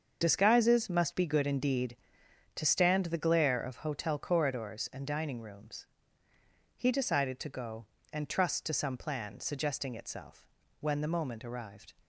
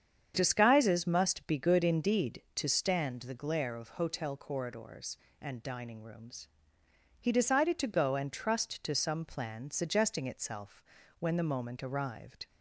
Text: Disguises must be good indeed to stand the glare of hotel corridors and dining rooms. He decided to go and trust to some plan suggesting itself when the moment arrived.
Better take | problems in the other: second | loses the start of "Disguises"; at 0.2 s; 30 ms // starts louder than the rest; until 1.2 s; 6.5 dB; strong in the second // pauses between "itself" and "when"; slight; at 10.4 s; 0.36 s long; slight in the second

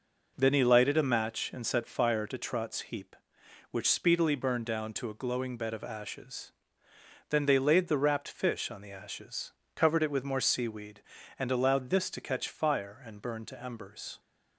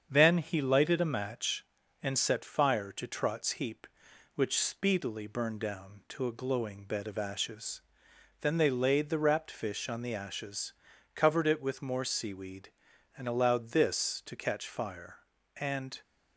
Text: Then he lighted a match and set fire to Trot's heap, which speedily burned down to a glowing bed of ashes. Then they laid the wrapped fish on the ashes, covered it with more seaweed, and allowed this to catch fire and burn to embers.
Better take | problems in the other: first | starts louder than the rest; strong; until 1.1 s; 7.5 dB // stops before "burn to embers"; at 16.0 s

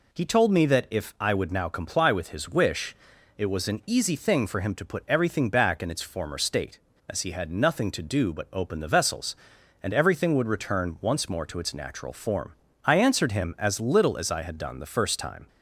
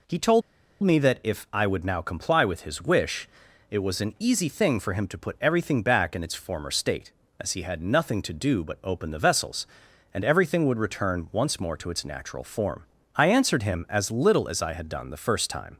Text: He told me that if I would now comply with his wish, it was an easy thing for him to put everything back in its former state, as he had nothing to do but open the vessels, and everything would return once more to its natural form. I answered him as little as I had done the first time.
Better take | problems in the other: first | pauses between "told" and "me"; at 0.4 s; 0.42 s long

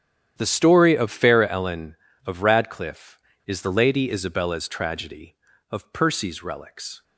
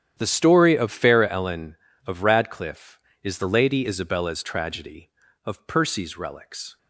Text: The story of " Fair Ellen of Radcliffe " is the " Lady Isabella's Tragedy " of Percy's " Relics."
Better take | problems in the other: neither | starts louder than the rest; strong; the same in both

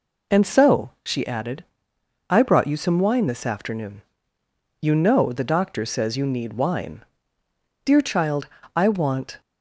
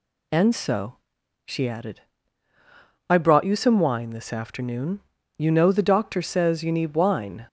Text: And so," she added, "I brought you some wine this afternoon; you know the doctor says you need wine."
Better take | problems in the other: second | goes on to say "Dear child I want"; from 7.8 s on; 1.5 s long

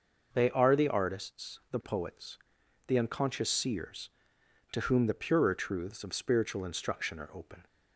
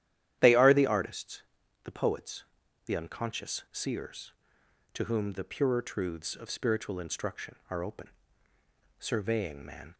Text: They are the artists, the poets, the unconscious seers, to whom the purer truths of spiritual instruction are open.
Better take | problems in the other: first | starts louder than the rest; strong; until 1.4 s; 11.5 dB // goes on to say "Surveying man"; noticeable; from 8.9 s on; 0.96 s long

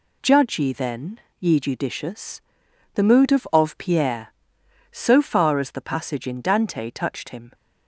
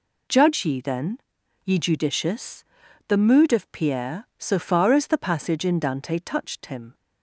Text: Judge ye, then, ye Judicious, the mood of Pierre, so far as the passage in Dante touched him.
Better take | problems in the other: second | says "of" twice; at 3.5 s

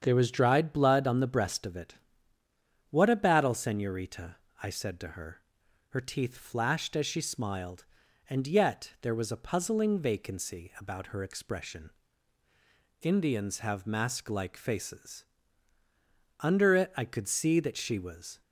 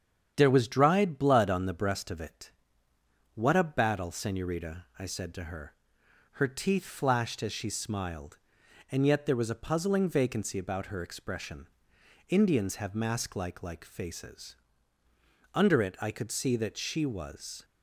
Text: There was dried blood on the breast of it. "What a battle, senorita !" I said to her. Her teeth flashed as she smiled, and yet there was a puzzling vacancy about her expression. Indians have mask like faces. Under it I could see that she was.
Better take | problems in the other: first | starts louder than the rest; strong; until 1.3 s; 8.5 dB; strong in the first // says "like" twice; at 13.6 s

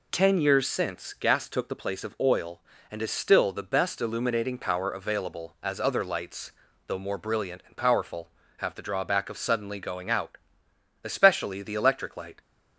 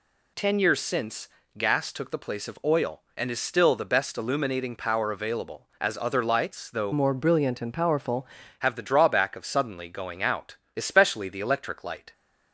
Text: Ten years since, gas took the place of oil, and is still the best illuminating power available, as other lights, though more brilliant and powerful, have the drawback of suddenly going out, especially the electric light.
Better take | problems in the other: first | changes voice from "more" to "powerful"; from 6.9 to 8.2 s; 1.3 s long

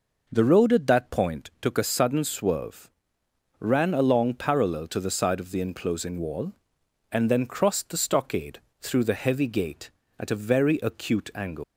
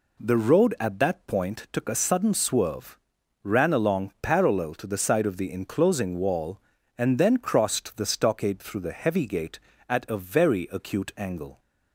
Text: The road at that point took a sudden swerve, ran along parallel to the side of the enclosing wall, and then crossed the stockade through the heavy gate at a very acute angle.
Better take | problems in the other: second | pauses between "stockade" and "through"; slight; at 8.5 s; 0.22 s long // leaves "angle" unfinished; at 11.6 s; 130 ms

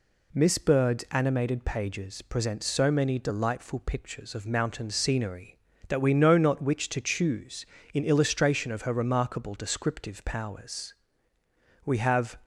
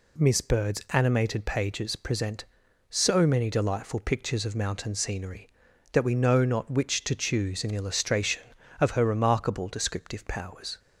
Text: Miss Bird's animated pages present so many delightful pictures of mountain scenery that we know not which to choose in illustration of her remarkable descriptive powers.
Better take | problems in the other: second | goes on to say "We have"; from 11.8 s on; 0.56 s long

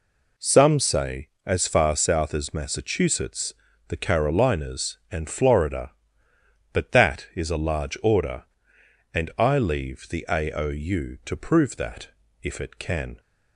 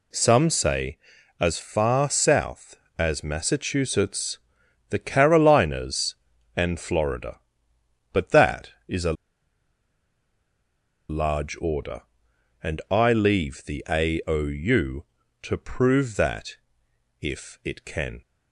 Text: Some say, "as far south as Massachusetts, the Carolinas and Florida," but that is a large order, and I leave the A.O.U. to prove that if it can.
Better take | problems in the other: first | pauses between "a" and "large"; strong; at 9.1 s; 1.9 s long // pauses between "that" and "if"; noticeable; at 16.5 s; 0.64 s long; slight in the first

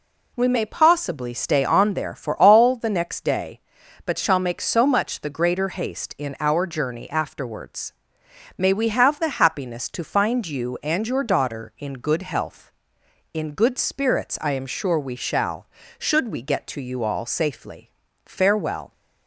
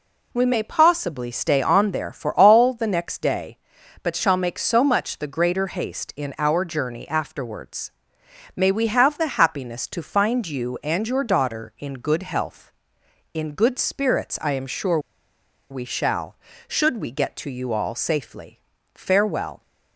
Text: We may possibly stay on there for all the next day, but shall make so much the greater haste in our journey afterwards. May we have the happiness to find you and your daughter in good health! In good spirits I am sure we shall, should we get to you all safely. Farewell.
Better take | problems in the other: first | pauses between "sure" and "we"; noticeable; at 14.9 s; 0.71 s long

